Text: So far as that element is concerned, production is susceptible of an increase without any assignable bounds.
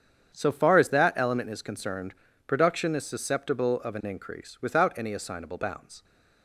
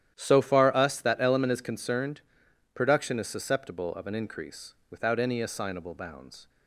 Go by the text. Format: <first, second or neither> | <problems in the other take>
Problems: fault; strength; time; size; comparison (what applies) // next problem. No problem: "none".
first | starts louder than the rest; strong; until 1.1 s; 11 dB; strong in the first // says "us" for "as"; at 0.7 s // pauses between "increase" and "without"; slight; at 4.7 s; 0.18 s long